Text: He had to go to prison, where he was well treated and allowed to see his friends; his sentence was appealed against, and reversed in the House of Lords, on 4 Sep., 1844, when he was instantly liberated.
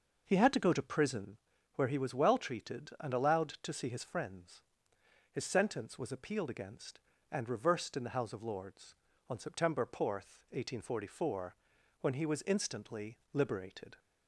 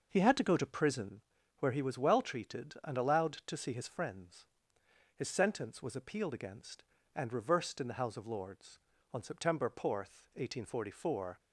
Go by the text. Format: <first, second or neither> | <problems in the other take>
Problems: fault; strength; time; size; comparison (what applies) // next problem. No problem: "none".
first | stops before "when he was instantly liberated"; at 11.3 s